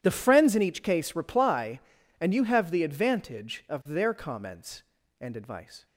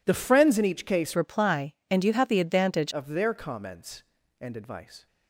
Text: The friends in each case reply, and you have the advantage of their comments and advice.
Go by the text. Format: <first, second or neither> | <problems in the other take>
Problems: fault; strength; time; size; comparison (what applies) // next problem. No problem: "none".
first | changes voice from "reply" to "advantage"; from 1.1 to 2.9 s; 1.8 s long